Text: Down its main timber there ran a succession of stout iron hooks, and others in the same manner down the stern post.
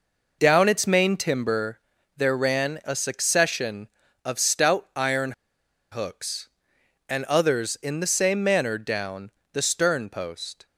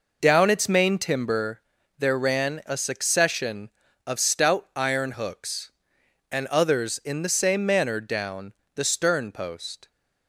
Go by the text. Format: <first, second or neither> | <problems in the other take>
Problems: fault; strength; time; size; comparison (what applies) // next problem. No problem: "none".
second | pauses between "timber" and "there"; at 1.7 s; 0.38 s long; also in the second // pauses between "iron" and "hooks"; noticeable; at 5.3 s; 0.59 s long // pauses between "down" and "the"; slight; at 9.2 s; 0.24 s long; slight in the second